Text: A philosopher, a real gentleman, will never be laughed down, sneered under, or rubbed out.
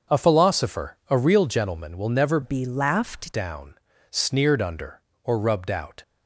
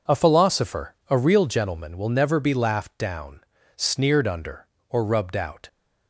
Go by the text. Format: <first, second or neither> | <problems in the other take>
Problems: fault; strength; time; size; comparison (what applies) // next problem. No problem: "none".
second | starts louder than the rest; until 1.2 s; 6.5 dB // changes voice from "be" to "laughed"; from 2.4 to 3.3 s; 0.9 s long